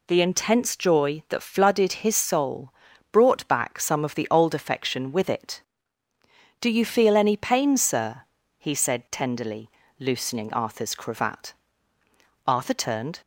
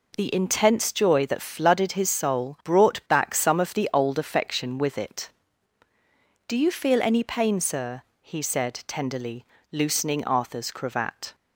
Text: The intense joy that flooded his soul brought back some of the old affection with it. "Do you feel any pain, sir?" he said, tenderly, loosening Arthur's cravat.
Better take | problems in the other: second | pauses between "soul" and "brought"; at 2.7 s; 0.40 s long // goes on to say "Arthur turned"; noticeable; from 12.4 s on; 0.72 s long

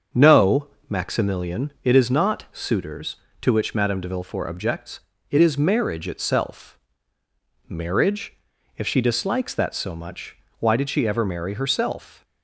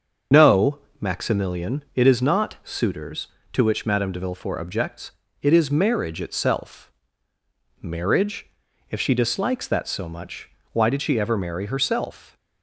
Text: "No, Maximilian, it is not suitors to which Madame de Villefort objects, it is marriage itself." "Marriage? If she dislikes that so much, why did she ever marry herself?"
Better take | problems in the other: first | loses the start of "No"; at 0.3 s; 65 ms // starts louder than the rest; until 1.5 s; 6.5 dB; also in the first

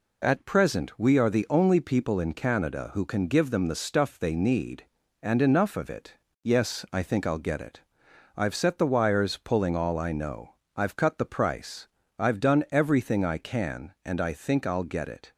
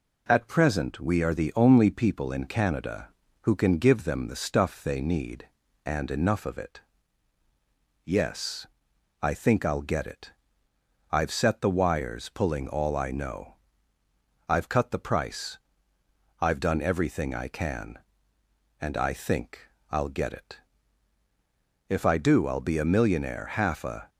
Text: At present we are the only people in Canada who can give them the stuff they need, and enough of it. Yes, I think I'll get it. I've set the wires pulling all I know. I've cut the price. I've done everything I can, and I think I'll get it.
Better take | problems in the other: first | pauses between "think" and "I'll"; slight; at 19.6 s; 0.22 s long // goes on to say "If I do I'll be a millionaire half a"; strong; from 21.8 s on; 2.2 s long

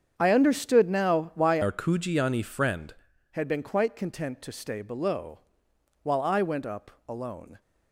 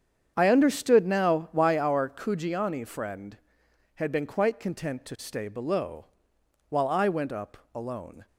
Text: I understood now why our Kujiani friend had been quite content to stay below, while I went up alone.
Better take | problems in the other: second | starts louder than the rest; strong; until 1.1 s; 7.5 dB; strong in the second // changes voice from "our" to "friend"; from 1.6 to 2.9 s; 1.3 s long // pauses between "up" and "alone"; slight; at 6.9 s; 0.18 s long; slight in the second

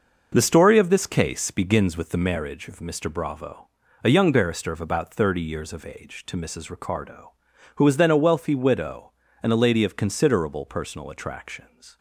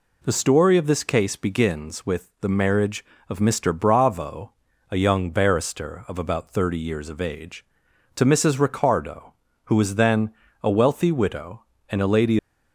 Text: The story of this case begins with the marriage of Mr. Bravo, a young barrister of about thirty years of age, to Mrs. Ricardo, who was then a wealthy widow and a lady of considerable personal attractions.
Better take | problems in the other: first | pauses between "then" and "a"; slight; at 10.2 s; 0.32 s long // stops before "of considerable personal attractions"; at 12.3 s

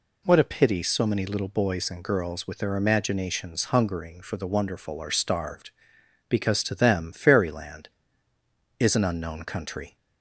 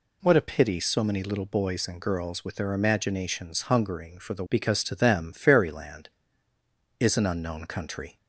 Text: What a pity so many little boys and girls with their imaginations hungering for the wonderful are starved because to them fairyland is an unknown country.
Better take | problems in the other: first | skips "wonderful are starved"; at 4.4 s

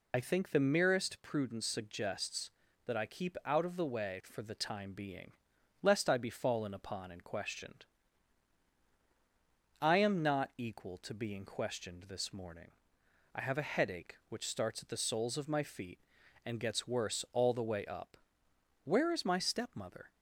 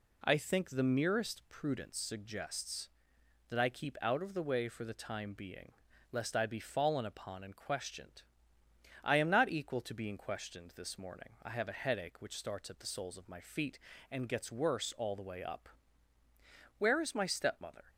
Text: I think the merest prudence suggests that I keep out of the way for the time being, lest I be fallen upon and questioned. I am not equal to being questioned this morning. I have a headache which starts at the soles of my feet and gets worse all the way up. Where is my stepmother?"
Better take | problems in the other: second | loses the start of "I"; at 0.1 s; 45 ms

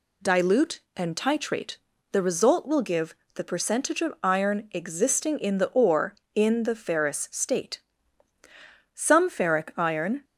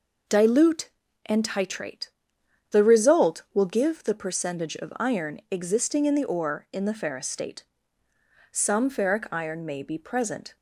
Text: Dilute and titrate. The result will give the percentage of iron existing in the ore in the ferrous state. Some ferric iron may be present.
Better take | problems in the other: second | pauses between "give" and "the"; slight; at 3.1 s; 0.22 s long // stops before "may be present"; at 10.2 s

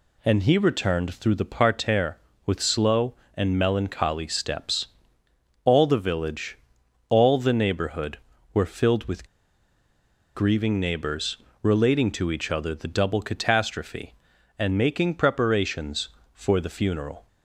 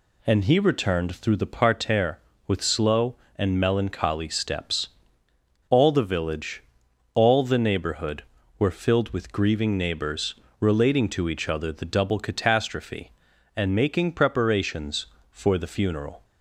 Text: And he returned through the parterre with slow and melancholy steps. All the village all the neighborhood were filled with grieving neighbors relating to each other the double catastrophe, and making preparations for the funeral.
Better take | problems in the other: second | pauses between "village" and "all"; noticeable; at 6.5 s; 0.56 s long; noticeable in the second // pauses between "with" and "grieving"; at 9.2 s; 1.0 s long // pauses between "neighbors" and "relating"; slight; at 11.3 s; 0.24 s long; slight in the second

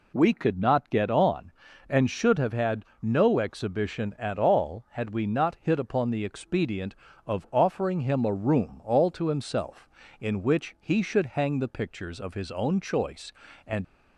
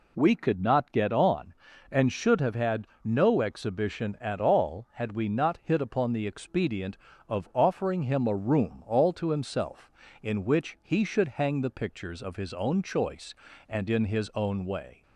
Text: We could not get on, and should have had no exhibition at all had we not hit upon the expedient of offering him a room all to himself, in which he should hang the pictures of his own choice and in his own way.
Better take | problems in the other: second | pauses between "had" and "no"; slight; at 2.8 s; 0.18 s long; slight in the second // stops before "in his own way"; at 13.8 s

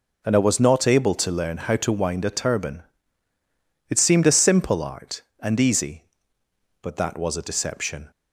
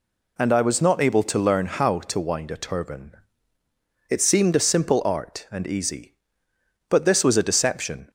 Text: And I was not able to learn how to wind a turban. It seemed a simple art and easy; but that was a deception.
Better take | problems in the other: first | says "this" for "that"; at 7.0 s

